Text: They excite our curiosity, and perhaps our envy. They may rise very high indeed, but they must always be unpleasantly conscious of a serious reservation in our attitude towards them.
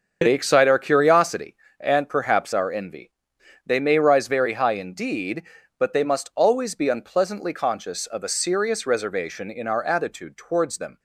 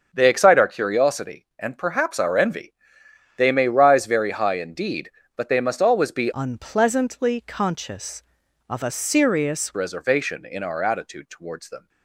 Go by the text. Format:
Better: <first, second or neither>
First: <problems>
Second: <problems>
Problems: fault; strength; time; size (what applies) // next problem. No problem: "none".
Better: first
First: starts louder than the rest; until 1.2 s; 6.5 dB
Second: starts louder than the rest; until 1.1 s; 7 dB // changes voice from "unpleasantly" to "serious"; from 6.3 to 9.7 s; 3.4 s long